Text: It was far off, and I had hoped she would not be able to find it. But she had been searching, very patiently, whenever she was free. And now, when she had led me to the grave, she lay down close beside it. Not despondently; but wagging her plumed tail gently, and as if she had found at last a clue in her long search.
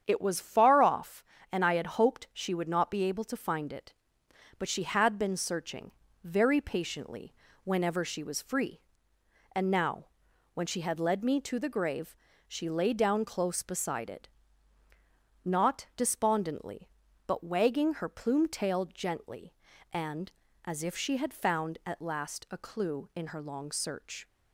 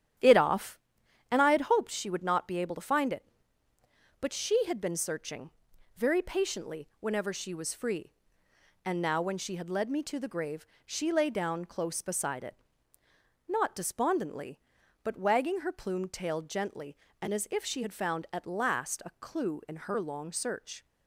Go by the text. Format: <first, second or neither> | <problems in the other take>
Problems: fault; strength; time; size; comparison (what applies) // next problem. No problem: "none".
first | starts louder than the rest; strong; until 1.6 s; 10.5 dB; strong in the first // skips "was far"; at 0.3 s